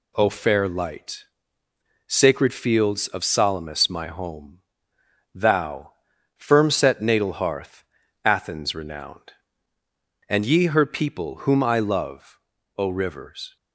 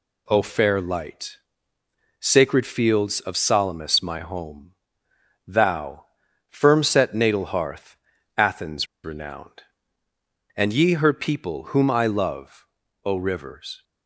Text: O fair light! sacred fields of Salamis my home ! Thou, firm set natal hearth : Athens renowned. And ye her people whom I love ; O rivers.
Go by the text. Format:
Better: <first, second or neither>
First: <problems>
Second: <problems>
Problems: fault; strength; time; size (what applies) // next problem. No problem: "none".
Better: first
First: none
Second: pauses between "Athens" and "renowned"; slight; at 8.8 s; 0.18 s long